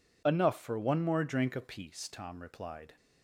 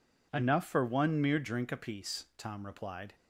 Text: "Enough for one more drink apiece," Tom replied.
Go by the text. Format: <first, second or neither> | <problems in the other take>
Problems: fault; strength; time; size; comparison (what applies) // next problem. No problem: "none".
first | says "mere" for "more"; at 1.2 s